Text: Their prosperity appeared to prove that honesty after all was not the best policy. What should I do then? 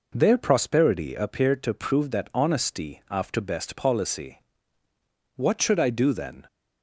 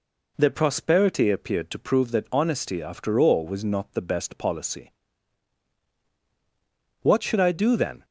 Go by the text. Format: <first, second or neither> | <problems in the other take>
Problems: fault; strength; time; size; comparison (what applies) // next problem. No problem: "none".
second | skips "all was not the"; at 3.4 s